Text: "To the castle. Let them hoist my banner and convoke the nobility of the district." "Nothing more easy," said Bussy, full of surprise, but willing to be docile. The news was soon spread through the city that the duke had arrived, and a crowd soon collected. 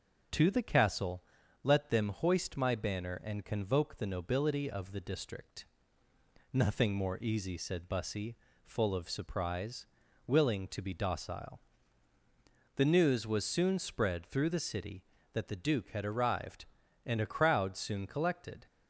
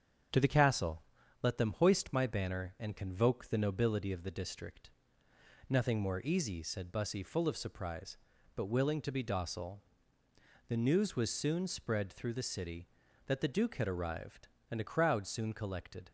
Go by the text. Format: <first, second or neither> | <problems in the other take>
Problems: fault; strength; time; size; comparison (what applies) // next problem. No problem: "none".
second | starts louder than the rest; until 1.7 s; 6.5 dB; strong in the second // skips "but"; at 10.0 s